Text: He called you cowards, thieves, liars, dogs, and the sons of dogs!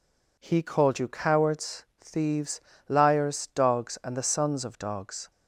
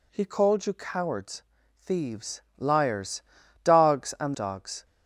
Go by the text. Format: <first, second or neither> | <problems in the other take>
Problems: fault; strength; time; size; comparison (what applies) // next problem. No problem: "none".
first | skips "the sons of"; at 4.3 s